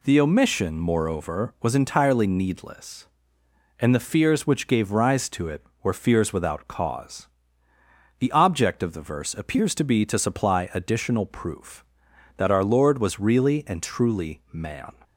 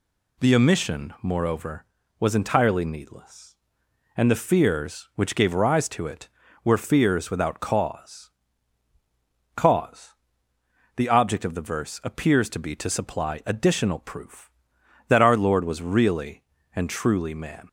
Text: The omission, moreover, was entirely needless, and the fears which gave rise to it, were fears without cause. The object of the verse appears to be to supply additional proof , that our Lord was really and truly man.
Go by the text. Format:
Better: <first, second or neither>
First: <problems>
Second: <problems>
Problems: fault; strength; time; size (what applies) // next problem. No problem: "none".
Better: first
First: none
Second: says "cause" twice; at 9.5 s